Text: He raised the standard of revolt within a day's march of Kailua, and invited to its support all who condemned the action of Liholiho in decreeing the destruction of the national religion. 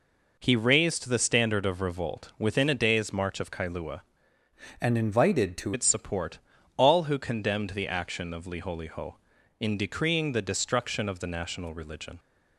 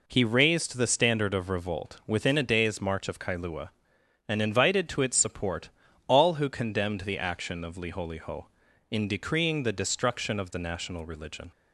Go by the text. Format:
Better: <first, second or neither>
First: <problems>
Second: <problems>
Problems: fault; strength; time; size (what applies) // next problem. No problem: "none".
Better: second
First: changes voice from "and" to "to"; from 4.8 to 5.7 s; 0.9 s long // pauses between "support" and "all"; slight; at 6.3 s; 0.36 s long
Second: pauses between "support" and "all"; slight; at 5.6 s; 0.36 s long